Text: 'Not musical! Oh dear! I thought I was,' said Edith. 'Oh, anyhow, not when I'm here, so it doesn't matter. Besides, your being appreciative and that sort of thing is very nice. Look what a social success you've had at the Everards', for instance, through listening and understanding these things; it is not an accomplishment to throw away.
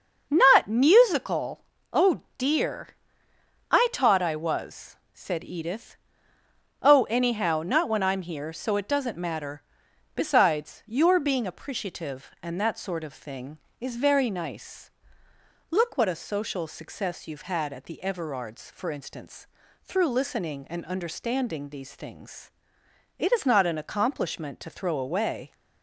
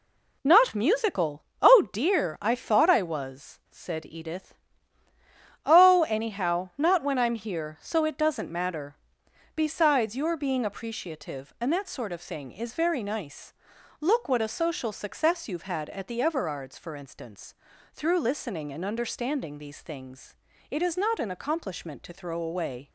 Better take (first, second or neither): second